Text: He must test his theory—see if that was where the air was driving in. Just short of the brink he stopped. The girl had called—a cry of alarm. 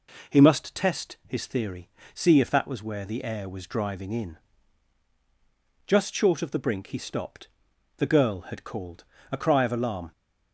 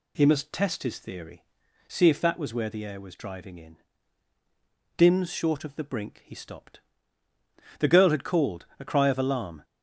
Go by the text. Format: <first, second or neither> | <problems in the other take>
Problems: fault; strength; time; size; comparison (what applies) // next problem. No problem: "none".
first | says "Dims" for "Just"; at 4.9 s